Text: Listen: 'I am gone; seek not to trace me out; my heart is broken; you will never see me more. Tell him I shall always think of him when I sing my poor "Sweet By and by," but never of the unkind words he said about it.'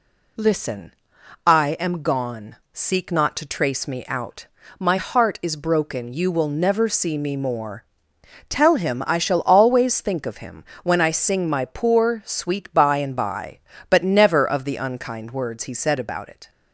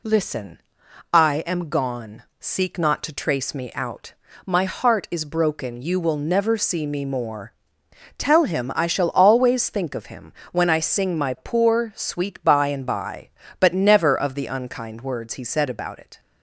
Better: neither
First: pauses between "him" and "when"; slight; at 10.6 s; 0.22 s long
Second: pauses between "him" and "when"; slight; at 10.3 s; 0.22 s long

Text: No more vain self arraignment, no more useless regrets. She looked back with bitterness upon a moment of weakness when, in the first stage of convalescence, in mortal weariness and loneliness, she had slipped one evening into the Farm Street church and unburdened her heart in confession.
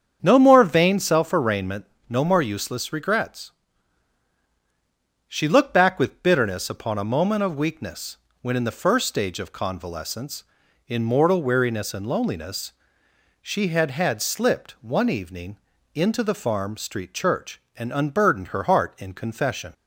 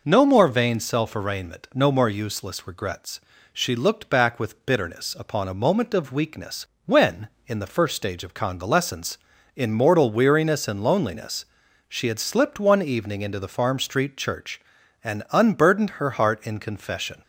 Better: second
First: starts louder than the rest; strong; until 1.2 s; 7.5 dB // pauses between "weakness" and "when"; slight; at 8.1 s; 0.26 s long // says "had" twice; at 13.9 s // pauses between "evening" and "into"; at 15.5 s; 0.38 s long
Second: pauses between "weakness" and "when"; slight; at 6.6 s; 0.20 s long

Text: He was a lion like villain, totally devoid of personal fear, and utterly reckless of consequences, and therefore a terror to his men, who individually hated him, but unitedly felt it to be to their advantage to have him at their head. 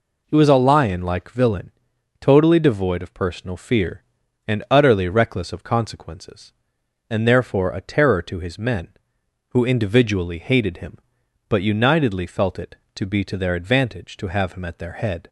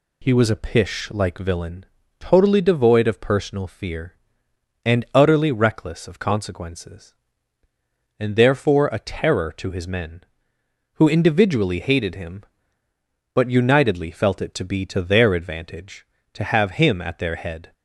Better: first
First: none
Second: says "pish" for "lion"; at 0.5 s

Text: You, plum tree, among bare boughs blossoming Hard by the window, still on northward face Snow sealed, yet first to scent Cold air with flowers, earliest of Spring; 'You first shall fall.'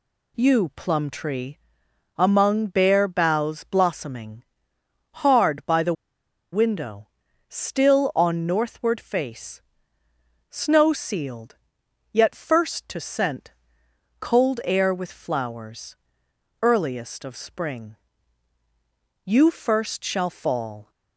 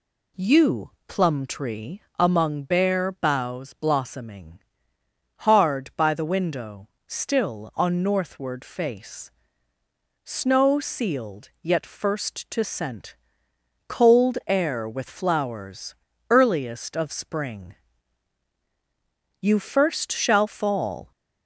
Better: second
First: pauses between "blossoming" and "Hard"; noticeable; at 4.4 s; 0.80 s long // pauses between "the" and "window"; noticeable; at 5.9 s; 0.59 s long // pauses between "face" and "Snow"; noticeable; at 9.6 s; 0.88 s long // pauses between "scent" and "Cold"; noticeable; at 13.5 s; 0.68 s long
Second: pauses between "blossoming" and "Hard"; noticeable; at 4.5 s; 0.80 s long // pauses between "face" and "Snow"; noticeable; at 9.3 s; 0.94 s long // pauses between "scent" and "Cold"; noticeable; at 13.1 s; 0.72 s long

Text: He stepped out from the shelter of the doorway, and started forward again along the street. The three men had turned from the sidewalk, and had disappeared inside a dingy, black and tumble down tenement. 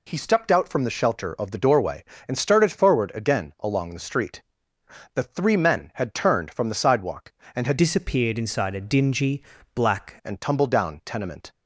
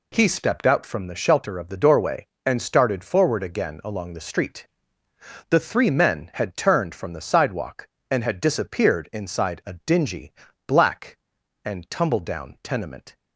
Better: second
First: changes voice from "disappeared" to "black"; from 7.7 to 10.1 s; 2.4 s long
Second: none

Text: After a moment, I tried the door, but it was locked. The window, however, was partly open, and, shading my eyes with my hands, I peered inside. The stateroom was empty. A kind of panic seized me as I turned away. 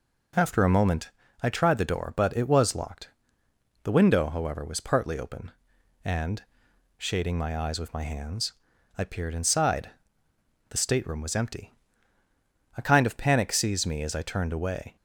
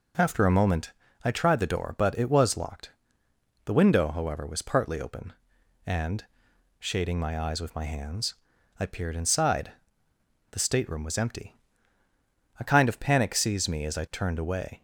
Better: neither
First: none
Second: none

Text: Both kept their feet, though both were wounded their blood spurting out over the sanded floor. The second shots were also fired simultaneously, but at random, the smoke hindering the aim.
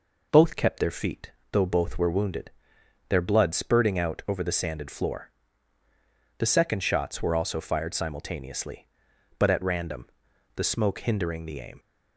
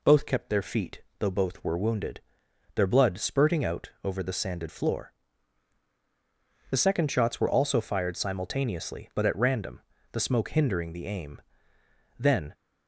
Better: first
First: pauses between "wounded" and "their"; noticeable; at 2.5 s; 0.58 s long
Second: pauses between "wounded" and "their"; noticeable; at 2.2 s; 0.54 s long // goes on to say "Then"; slight; from 12.1 s on; 0.34 s long

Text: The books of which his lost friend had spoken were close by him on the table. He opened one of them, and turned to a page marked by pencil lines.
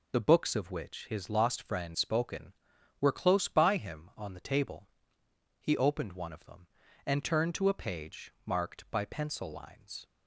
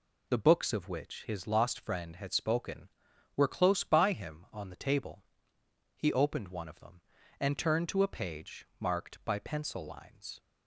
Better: second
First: skips "had"; at 1.9 s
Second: none

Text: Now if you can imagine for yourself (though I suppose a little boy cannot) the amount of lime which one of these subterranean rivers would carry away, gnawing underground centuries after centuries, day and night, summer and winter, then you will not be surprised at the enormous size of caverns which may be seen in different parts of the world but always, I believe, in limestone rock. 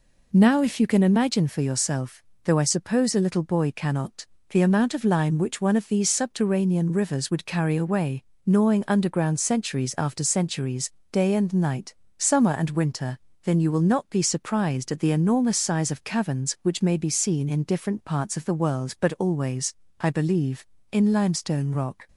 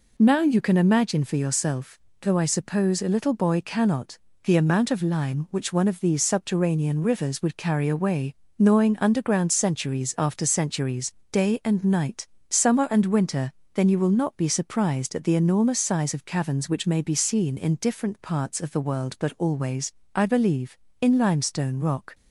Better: first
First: none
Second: skips "if"; at 0.4 s

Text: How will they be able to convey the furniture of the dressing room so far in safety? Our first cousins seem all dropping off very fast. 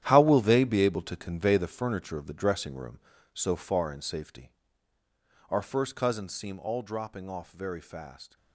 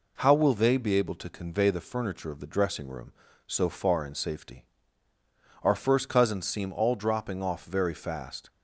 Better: second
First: gets quieter; strong; throughout; 11.5 dB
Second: none

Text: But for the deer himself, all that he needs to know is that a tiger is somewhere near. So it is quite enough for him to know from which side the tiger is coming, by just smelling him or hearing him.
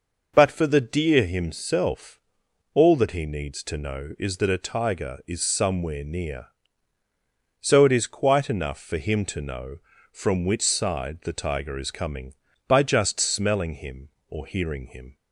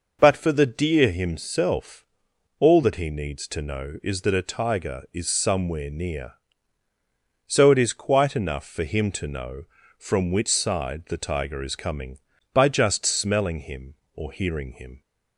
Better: neither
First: none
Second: none

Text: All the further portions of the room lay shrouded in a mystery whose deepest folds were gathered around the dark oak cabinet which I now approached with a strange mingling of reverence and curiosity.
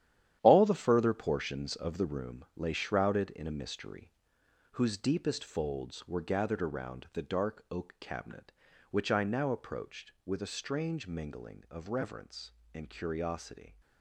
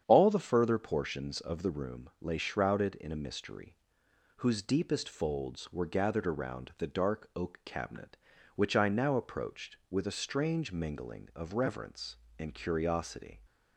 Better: second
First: gets quieter; strong; throughout; 9 dB // starts louder than the rest; strong; until 1.4 s; 11 dB // pauses between "mystery" and "whose"; noticeable; at 4.1 s; 0.60 s long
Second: starts louder than the rest; strong; until 1.0 s; 8.5 dB // pauses between "mystery" and "whose"; noticeable; at 3.7 s; 0.60 s long

